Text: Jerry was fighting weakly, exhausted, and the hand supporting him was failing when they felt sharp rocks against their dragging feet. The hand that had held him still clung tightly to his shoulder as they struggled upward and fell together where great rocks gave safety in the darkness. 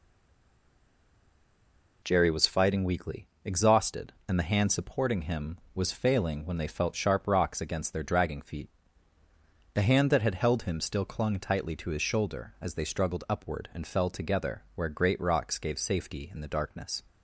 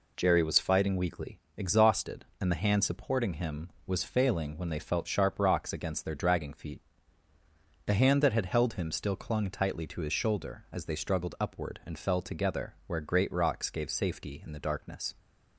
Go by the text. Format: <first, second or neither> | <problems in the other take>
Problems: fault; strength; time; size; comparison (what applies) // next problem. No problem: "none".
second | stays silent before the first word; noticeable; until 2.0 s; 2.0 s long